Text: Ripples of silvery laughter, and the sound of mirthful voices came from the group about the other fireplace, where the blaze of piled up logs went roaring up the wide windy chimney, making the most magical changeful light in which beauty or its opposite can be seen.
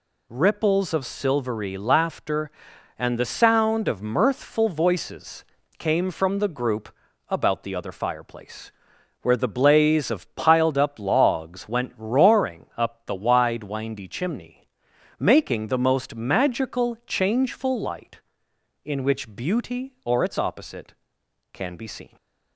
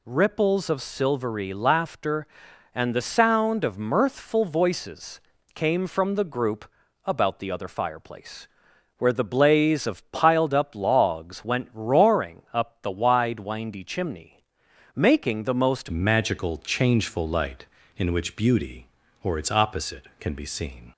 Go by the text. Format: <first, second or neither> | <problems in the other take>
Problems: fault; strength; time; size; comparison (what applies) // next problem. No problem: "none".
first | pauses between "voices" and "came"; slight; at 5.1 s; 0.34 s long; slight in the first // pauses between "group" and "about"; at 6.6 s; 0.38 s long; also in the first // changes voice at "magical"; from 15.8 s on; 5.1 s long